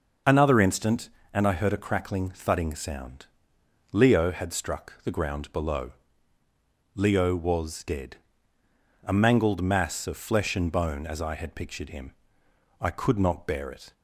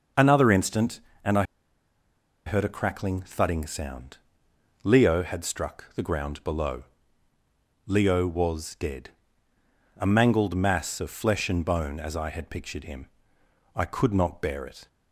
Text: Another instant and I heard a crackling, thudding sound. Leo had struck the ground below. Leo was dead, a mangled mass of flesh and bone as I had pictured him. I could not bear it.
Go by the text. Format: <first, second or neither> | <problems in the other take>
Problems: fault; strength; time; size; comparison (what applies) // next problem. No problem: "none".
first | starts louder than the rest; noticeable; until 1.4 s; 6 dB; noticeable in the first // pauses between "I" and "heard"; at 1.4 s; 1.0 s long